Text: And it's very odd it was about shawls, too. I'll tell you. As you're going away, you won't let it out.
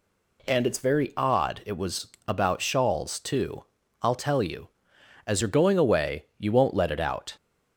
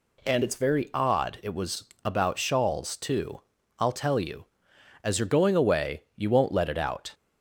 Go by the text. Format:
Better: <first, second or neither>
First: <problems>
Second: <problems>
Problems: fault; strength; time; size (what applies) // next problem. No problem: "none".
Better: neither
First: pauses between "was" and "about"; slight; at 2.0 s; 0.20 s long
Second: pauses between "was" and "about"; slight; at 1.8 s; 0.20 s long